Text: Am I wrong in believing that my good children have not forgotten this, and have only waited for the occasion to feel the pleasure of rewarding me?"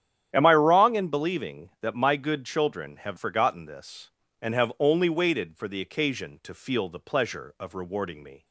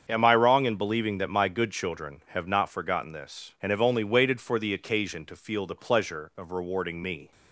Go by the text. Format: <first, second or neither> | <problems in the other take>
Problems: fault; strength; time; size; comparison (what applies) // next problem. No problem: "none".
second | starts louder than the rest; strong; until 1.3 s; 10 dB; strong in the second // skips "not"; at 3.1 s